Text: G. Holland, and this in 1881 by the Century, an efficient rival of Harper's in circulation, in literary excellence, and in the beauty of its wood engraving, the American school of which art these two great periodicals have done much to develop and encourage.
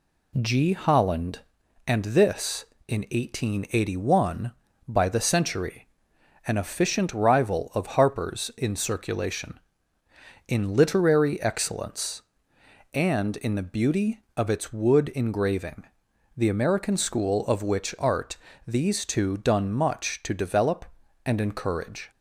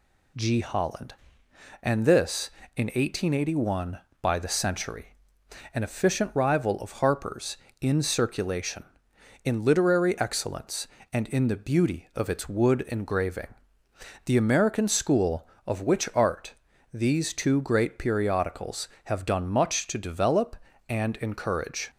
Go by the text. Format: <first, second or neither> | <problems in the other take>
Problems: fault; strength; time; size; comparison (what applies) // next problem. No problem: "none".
second | pauses between "art" and "these"; slight; at 18.3 s; 0.30 s long; also in the second // skips "great periodicals have"; at 19.3 s